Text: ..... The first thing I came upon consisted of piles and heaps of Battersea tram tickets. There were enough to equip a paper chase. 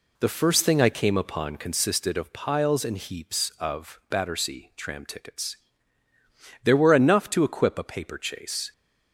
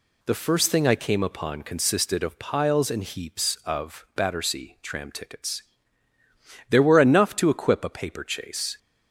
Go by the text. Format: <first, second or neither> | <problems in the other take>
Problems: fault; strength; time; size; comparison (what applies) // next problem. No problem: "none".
second | starts louder than the rest; slight; until 1.8 s; 2.5 dB